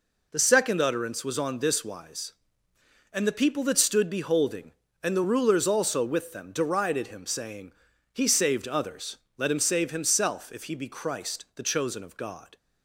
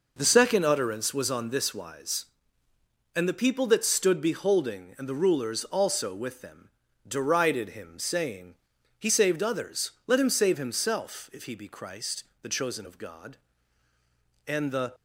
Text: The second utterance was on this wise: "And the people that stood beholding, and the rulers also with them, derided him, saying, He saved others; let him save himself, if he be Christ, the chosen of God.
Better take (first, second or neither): first